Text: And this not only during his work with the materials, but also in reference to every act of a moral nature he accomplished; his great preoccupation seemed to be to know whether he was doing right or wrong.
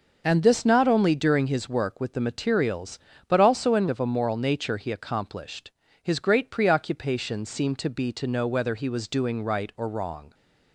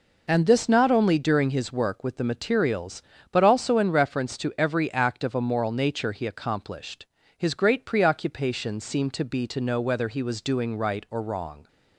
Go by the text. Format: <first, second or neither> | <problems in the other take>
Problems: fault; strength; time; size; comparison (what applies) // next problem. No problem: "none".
second | starts louder than the rest; noticeable; until 1.2 s; 6 dB // skips "reference to every act"; at 3.8 s